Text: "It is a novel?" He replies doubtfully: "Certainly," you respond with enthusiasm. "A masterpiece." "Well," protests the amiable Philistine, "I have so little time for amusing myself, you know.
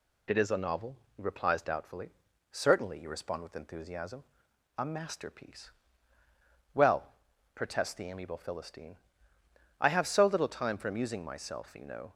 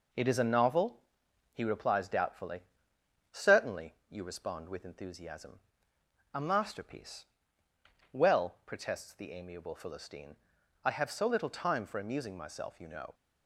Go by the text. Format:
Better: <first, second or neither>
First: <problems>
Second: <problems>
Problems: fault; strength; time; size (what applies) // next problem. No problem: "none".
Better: first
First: none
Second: gets quieter; noticeable; throughout; 4 dB